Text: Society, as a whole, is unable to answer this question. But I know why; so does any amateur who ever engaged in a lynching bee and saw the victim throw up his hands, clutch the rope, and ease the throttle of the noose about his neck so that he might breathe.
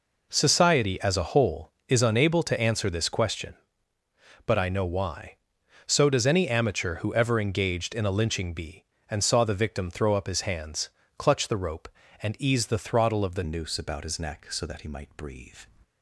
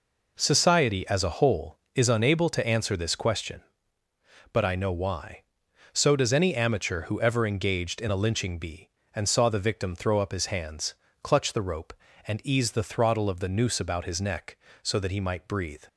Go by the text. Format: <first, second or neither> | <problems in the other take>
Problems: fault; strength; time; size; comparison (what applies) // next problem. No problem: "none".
second | changes voice at "noose"; from 13.4 s on; 2.1 s long